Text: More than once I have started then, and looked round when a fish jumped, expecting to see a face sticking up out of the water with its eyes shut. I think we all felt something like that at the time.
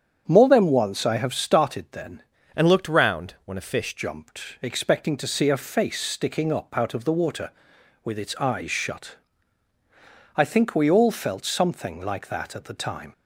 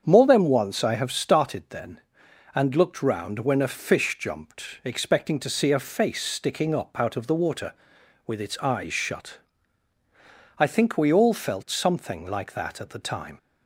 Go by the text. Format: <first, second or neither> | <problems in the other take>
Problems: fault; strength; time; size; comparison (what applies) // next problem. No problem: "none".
second | starts louder than the rest; strong; until 1.2 s; 7.5 dB; strong in the second // changes voice from "and" to "fish"; from 2.5 to 3.9 s; 1.4 s long